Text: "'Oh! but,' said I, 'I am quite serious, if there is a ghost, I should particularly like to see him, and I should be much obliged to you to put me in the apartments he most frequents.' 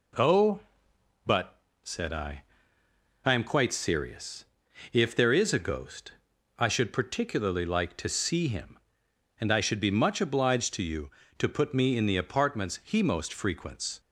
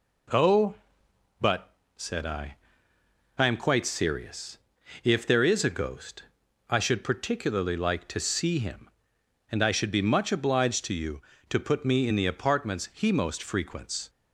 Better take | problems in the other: neither | none

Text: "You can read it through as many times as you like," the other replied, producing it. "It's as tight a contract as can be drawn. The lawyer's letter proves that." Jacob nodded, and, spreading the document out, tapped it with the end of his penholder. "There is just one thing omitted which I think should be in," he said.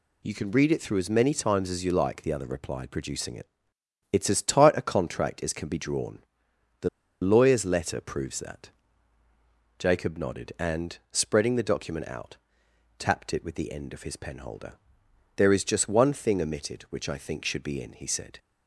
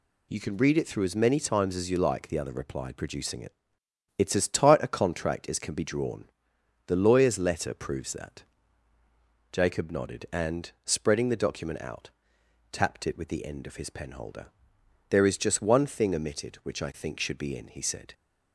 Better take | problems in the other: second | pauses between "The" and "lawyer's"; slight; at 6.8 s; 0.33 s long

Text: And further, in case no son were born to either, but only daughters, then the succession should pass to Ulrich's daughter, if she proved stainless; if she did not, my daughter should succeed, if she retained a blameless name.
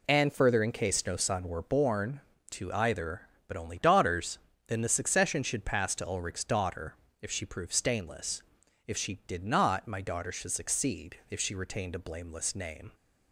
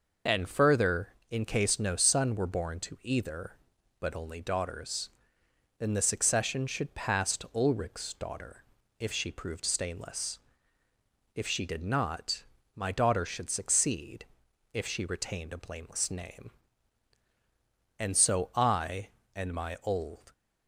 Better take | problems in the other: first | goes on to say "And so I and my old"; strong; from 17.9 s on; 2.3 s long

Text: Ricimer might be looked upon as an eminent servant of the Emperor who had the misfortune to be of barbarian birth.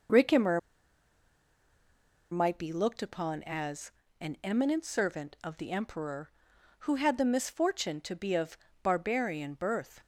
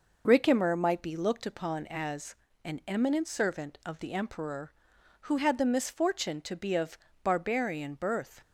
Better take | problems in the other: second | pauses between "Ricimer" and "might"; strong; at 0.5 s; 1.7 s long // pauses between "as" and "an"; slight; at 3.9 s; 0.30 s long; slight in the second // pauses between "of" and "barbarian"; slight; at 8.5 s; 0.28 s long; slight in the second

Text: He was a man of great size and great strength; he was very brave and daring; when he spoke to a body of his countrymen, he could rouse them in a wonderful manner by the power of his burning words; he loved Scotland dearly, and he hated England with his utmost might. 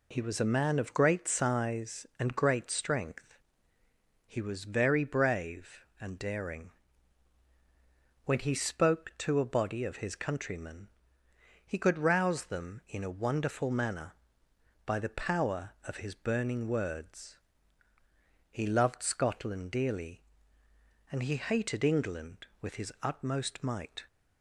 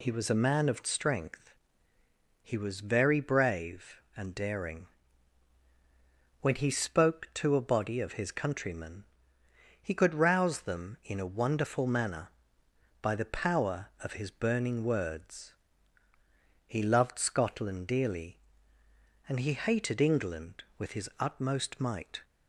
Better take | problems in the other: first | skips "great size and great"; at 0.8 s

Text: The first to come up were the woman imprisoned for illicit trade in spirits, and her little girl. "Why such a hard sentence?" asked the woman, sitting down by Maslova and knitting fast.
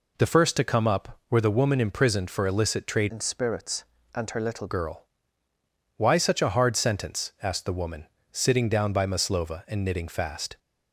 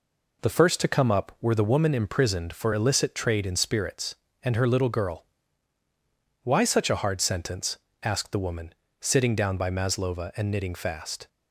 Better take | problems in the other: second | changes voice from "in" to "little"; from 3.0 to 4.6 s; 1.6 s long

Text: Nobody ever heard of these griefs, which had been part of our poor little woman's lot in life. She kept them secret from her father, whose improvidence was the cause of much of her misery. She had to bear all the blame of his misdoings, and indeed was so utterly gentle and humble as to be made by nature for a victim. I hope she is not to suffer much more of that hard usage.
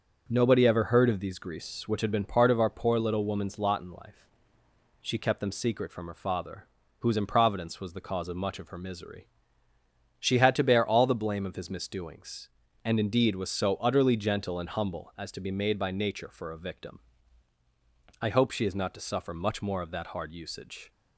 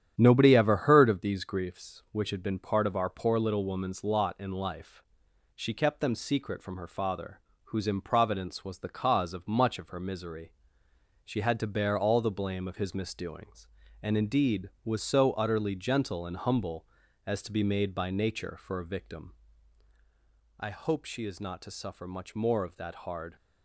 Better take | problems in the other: first | starts louder than the rest; strong; until 1.1 s; 9.5 dB; also in the first // stops before "usage"; at 23.3 s

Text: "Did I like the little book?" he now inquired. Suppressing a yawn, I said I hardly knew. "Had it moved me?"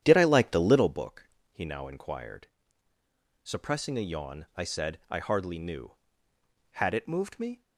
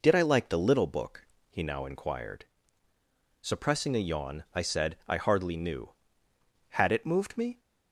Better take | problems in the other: second | starts louder than the rest; strong; until 1.0 s; 10 dB

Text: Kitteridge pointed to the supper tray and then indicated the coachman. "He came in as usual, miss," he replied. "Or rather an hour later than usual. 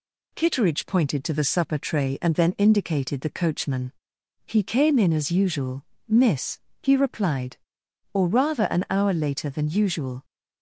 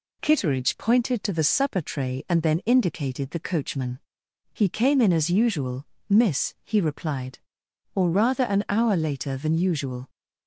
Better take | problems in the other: neither | none

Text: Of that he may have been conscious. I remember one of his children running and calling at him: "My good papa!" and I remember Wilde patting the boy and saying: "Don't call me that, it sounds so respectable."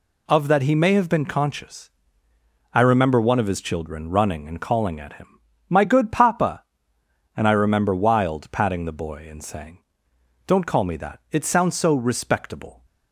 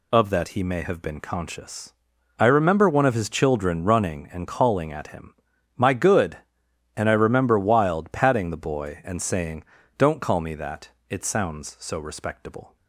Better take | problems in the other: first | skips "papa"; at 6.6 s

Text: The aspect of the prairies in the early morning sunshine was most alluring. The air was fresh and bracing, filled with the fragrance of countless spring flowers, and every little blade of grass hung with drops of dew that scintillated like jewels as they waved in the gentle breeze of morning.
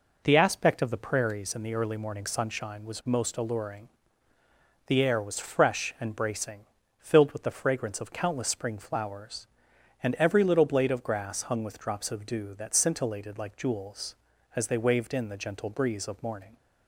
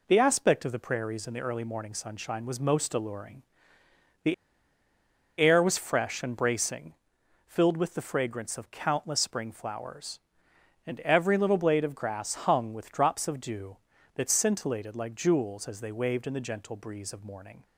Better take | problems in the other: first | pauses between "The" and "air"; at 4.3 s; 1.0 s long

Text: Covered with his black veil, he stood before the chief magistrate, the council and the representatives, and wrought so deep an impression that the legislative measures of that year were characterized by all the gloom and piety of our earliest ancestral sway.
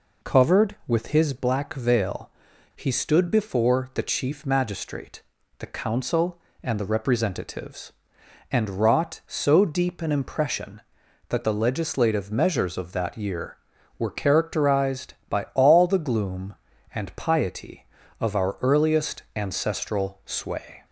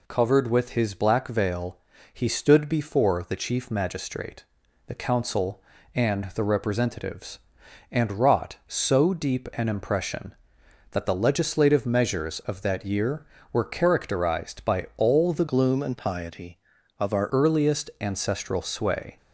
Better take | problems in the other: first | changes voice from "gloom" to "our"; from 15.4 to 17.2 s; 1.8 s long

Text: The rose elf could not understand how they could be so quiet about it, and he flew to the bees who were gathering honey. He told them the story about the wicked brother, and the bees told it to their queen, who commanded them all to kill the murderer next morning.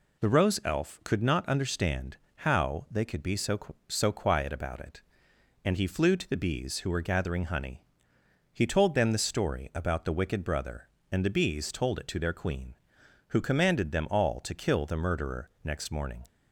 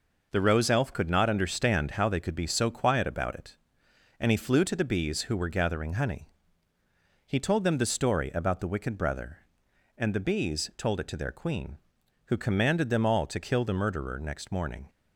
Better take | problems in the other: second | pauses between "understand" and "how"; slight; at 2.1 s; 0.20 s long // says "so" twice; at 3.8 s

